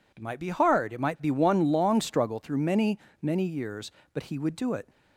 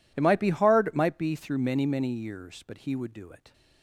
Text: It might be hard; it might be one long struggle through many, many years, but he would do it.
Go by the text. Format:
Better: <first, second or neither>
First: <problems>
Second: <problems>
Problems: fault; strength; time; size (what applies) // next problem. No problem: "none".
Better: first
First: none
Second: skips "one long struggle"; at 1.3 s